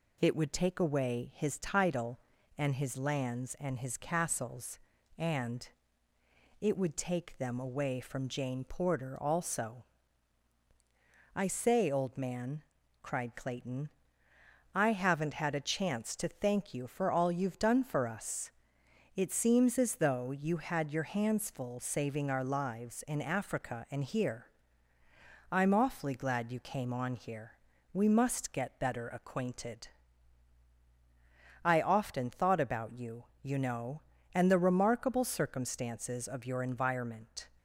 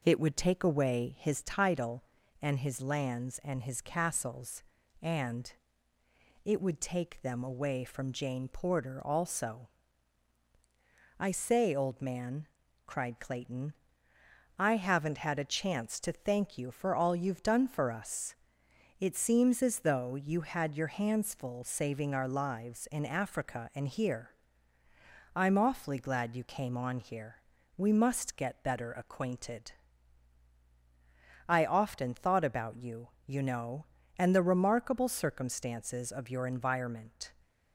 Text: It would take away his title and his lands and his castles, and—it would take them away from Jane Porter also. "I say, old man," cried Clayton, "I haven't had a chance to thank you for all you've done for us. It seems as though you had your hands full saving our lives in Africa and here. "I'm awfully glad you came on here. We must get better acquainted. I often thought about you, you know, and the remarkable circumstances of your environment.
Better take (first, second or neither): first